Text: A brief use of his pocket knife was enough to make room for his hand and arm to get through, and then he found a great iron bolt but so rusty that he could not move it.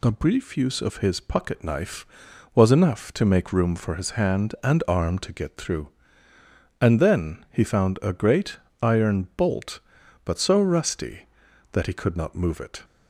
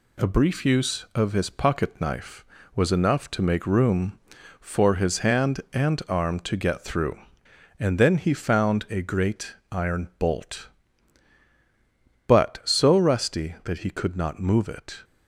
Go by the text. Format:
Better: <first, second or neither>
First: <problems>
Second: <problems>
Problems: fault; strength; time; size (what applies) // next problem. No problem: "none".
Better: first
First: pauses between "great" and "iron"; slight; at 8.5 s; 0.24 s long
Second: gets quieter; slight; throughout; 3 dB // pauses between "great" and "iron"; slight; at 9.5 s; 0.16 s long